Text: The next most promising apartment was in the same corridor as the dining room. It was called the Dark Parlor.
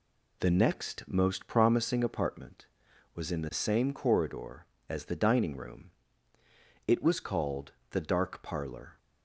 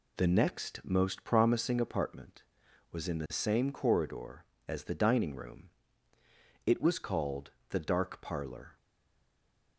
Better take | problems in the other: first | pauses between "called" and "the"; slight; at 7.5 s; 0.18 s long; slight in the first // stays silent after the last word; from 8.7 s on; 1.0 s long

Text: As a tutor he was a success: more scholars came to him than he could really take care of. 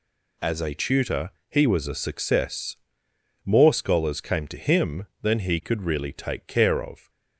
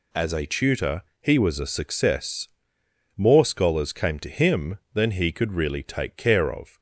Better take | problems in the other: neither | pauses between "tutor" and "he"; slight; the same in both

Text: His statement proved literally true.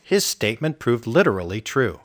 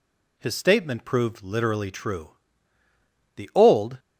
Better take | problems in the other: first | goes on to say "The old"; noticeable; from 3.3 s on; 0.62 s long

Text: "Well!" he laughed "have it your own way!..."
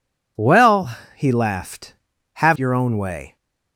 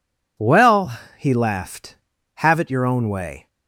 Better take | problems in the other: second | skips "it"; at 2.5 s

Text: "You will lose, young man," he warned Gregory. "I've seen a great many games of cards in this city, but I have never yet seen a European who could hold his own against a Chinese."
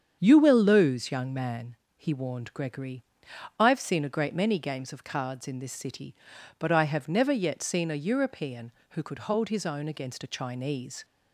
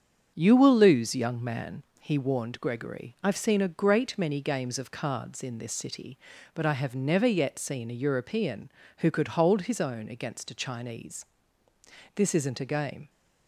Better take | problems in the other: first | starts louder than the rest; strong; until 1.3 s; 7.5 dB; strong in the first // goes on to say "This isn't a game"; noticeable; from 12.1 s on; 0.94 s long

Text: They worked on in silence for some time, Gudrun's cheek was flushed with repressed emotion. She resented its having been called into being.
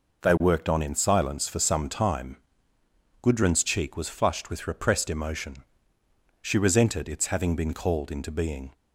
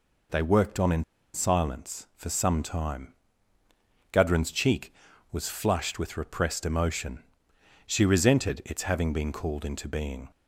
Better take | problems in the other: first | pauses between "in" and "silence"; slight; at 1.0 s; 0.31 s long

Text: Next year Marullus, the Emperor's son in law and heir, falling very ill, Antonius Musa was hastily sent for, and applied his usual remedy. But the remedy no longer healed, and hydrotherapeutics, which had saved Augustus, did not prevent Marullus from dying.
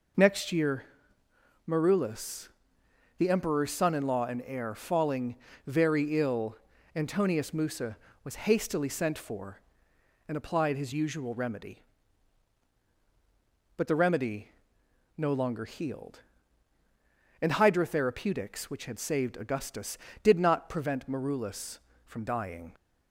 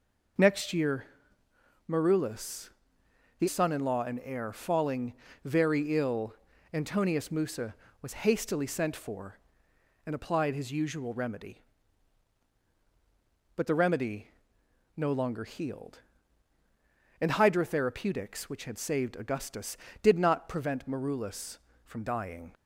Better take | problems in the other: first | pauses between "year" and "Marullus"; noticeable; at 1.0 s; 0.84 s long; noticeable in the first // skips "Emperor's"; at 3.4 s // pauses between "falling" and "very"; slight; at 5.1 s; 0.30 s long; slight in the first // pauses between "remedy" and "no"; noticeable; at 14.2 s; 0.68 s long; noticeable in the first

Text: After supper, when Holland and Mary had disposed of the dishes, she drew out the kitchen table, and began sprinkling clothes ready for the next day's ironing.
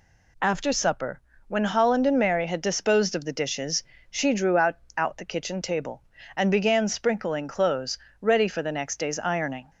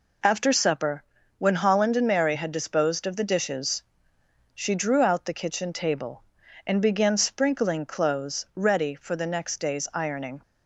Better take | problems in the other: second | says "out" twice; at 4.9 s // pauses between "clothes" and "ready"; slight; at 7.9 s; 0.22 s long

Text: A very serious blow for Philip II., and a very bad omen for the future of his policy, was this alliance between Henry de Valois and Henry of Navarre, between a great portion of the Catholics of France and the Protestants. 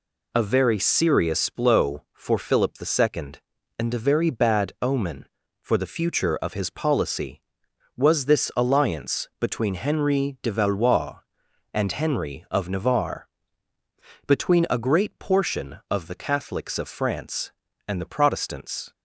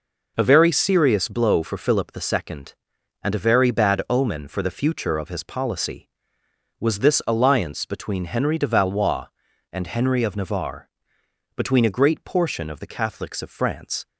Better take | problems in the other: first | stops before "and the Protestants"; at 14.0 s

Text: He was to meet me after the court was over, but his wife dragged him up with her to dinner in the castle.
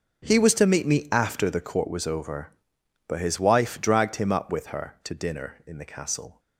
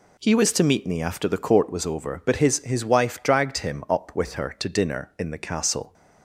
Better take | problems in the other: first | says "his" twice; at 2.6 s

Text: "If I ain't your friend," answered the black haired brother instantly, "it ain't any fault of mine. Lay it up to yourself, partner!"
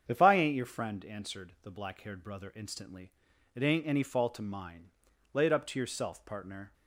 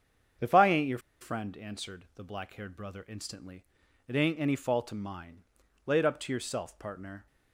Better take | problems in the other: first | starts louder than the rest; strong; until 1.6 s; 7.5 dB; strong in the first // pauses between "your" and "friend"; slight; at 0.9 s; 0.22 s long

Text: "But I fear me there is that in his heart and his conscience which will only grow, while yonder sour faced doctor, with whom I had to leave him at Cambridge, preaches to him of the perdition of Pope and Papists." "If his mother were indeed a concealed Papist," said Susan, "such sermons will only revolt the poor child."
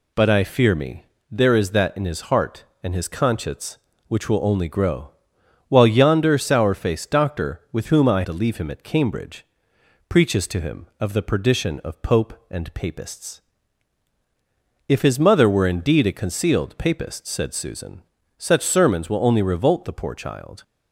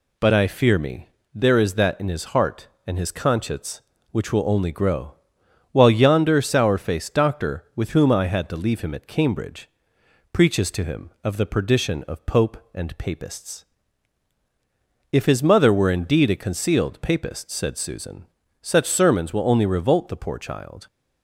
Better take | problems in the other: second | pauses between "me" and "there"; slight; at 1.0 s; 0.26 s long; slight in the second // skips "had"; at 8.2 s

